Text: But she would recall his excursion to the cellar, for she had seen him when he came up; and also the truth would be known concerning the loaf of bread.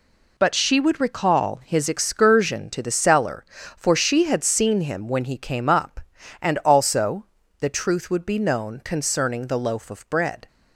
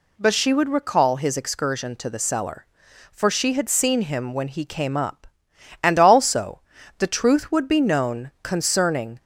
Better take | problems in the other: first | pauses between "also" and "the"; at 6.6 s; 0.38 s long; slight in the first // stops before "the loaf of bread"; at 9.1 s

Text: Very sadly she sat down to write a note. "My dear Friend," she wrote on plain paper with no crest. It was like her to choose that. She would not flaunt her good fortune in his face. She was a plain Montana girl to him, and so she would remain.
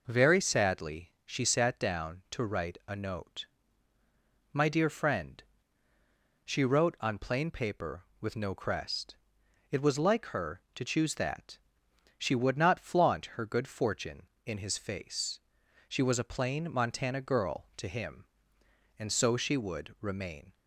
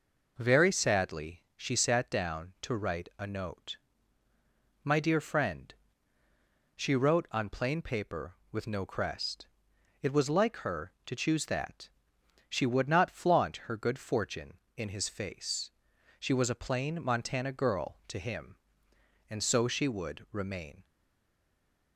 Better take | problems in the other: first | stays silent after the last word; from 20.8 s on; 1.1 s long

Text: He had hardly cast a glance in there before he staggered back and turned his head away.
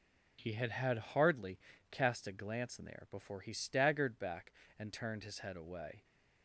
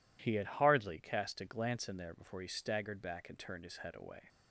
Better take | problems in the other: second | says "had" twice; at 0.7 s // pauses between "hardly" and "cast"; slight; at 1.5 s; 0.34 s long

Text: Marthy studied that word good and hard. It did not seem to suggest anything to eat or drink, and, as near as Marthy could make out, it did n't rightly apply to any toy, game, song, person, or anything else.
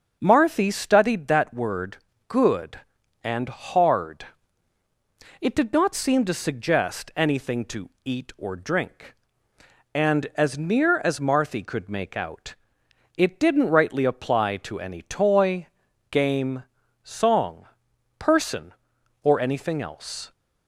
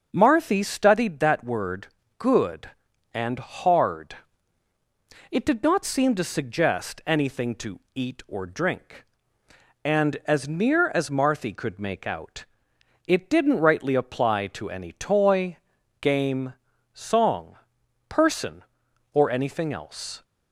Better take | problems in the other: neither | starts louder than the rest; the same in both // pauses between "word" and "good"; slight; the same in both // pauses between "to" and "eat"; slight; the same in both

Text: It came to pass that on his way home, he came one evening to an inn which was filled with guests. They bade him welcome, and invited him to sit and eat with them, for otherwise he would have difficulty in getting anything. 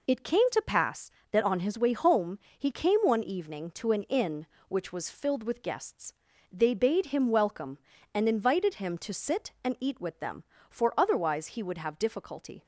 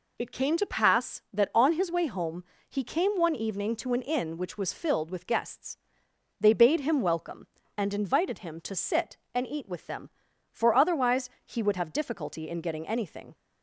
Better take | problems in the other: second | stops before "in getting anything"; at 12.6 s

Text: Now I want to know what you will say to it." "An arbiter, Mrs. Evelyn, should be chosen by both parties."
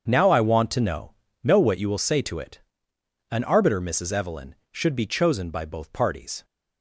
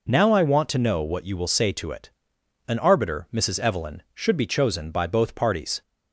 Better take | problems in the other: second | starts louder than the rest; until 1.0 s; 7 dB // says "know" twice; at 1.4 s

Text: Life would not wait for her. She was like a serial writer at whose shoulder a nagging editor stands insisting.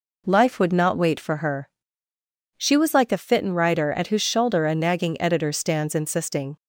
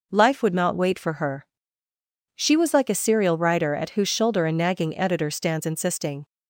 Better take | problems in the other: second | says "fitten" for "serial"; at 3.1 s

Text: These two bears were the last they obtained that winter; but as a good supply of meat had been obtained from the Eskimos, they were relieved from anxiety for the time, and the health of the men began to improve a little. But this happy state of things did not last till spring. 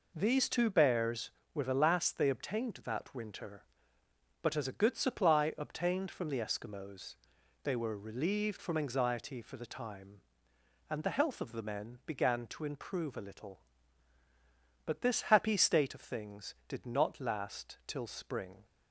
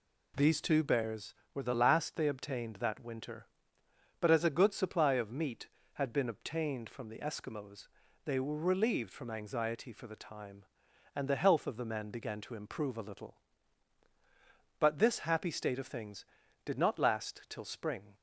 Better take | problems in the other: second | skips "of meat had been"; at 5.5 s

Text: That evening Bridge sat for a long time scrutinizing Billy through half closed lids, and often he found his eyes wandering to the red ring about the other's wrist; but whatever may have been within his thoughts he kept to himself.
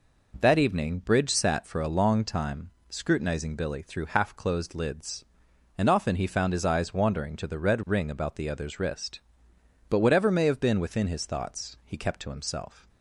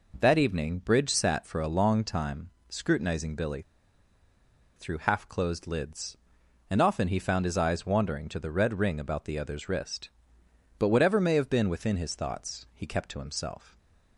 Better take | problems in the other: first | pauses between "time" and "scrutinizing"; slight; at 2.4 s; 0.20 s long; slight in the first // pauses between "Billy" and "through"; at 3.6 s; 1.1 s long

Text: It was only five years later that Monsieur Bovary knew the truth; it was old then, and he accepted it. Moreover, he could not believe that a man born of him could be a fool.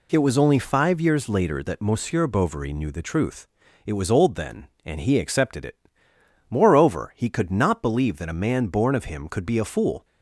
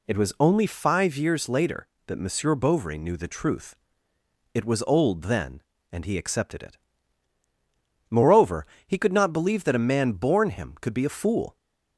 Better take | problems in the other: first | skips "of"; at 10.5 s

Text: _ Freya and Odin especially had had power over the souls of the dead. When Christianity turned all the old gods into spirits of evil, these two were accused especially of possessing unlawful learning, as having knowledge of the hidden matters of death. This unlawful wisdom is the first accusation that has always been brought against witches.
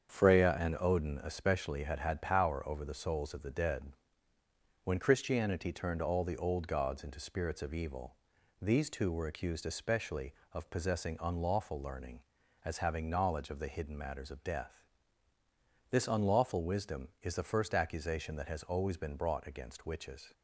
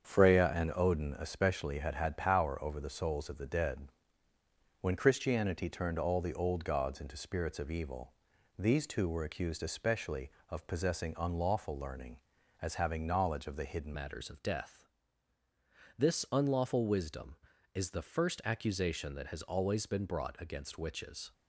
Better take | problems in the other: first | starts louder than the rest; strong; until 1.1 s; 7.5 dB; strong in the first // changes voice at "matters"; from 13.9 s on; 7.4 s long

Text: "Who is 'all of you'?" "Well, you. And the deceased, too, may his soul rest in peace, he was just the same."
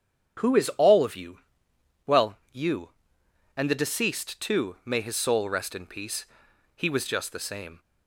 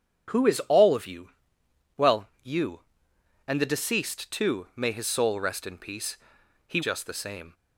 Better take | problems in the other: first | starts louder than the rest; strong; until 2.0 s; 8 dB; strong in the first // skips "was"; at 6.8 s

